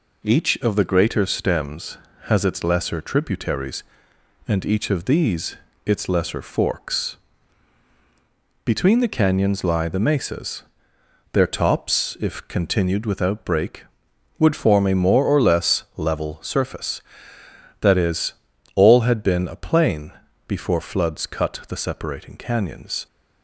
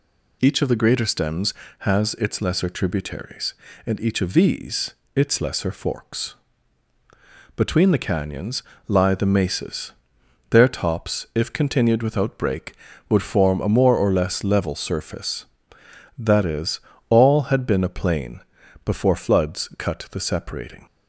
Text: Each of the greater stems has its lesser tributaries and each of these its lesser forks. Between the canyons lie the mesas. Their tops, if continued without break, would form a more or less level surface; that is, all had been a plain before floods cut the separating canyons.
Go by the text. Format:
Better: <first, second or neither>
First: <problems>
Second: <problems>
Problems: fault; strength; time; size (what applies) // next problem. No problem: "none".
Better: first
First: pauses between "these" and "its"; slight; at 5.5 s; 0.30 s long // pauses between "plain" and "before"; slight; at 20.1 s; 0.36 s long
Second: pauses between "these" and "its"; slight; at 4.9 s; 0.24 s long // pauses between "canyons" and "lie"; slight; at 8.6 s; 0.26 s long // pauses between "plain" and "before"; noticeable; at 18.3 s; 0.46 s long // stops before "canyons"; at 20.8 s